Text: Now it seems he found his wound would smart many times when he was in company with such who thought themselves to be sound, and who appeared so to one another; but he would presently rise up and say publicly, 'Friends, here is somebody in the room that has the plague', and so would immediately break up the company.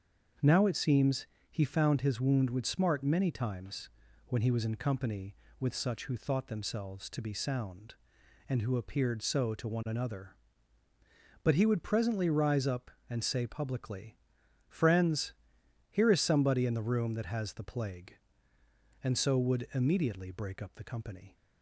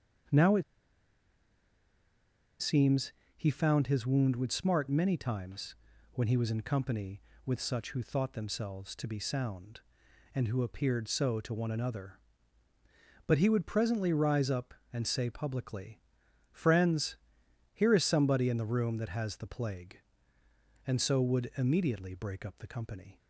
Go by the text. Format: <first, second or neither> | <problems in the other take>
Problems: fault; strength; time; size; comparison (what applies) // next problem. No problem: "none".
first | starts louder than the rest; until 3.5 s; 7 dB; strong in the first // pauses between "it" and "seems"; strong; at 0.6 s; 1.9 s long // pauses between "seems" and "he"; slight; at 3.1 s; 0.24 s long; slight in the first // pauses between "times" and "when"; at 5.7 s; 0.38 s long; also in the first